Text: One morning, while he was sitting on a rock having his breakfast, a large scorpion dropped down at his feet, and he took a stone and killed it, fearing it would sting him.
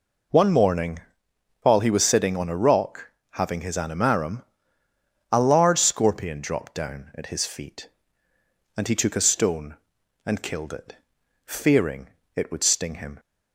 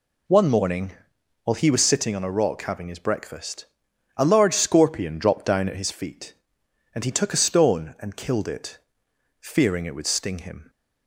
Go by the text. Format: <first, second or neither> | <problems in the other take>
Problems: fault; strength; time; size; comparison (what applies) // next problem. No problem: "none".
second | pauses between "rock" and "having"; slight; at 3.0 s; 0.22 s long // says "animarum" for "breakfast"; at 3.7 s // pauses between "fearing" and "it"; slight; at 12.0 s; 0.26 s long